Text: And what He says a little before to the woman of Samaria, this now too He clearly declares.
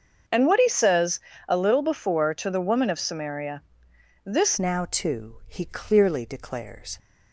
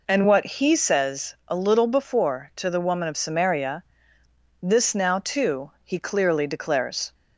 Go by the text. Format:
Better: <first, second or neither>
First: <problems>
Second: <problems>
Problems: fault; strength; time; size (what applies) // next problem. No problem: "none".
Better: second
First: starts louder than the rest; until 1.5 s; 6.5 dB // pauses between "says" and "a"; slight; at 1.2 s; 0.26 s long // changes voice at "now"; from 4.5 s on; 2.4 s long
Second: none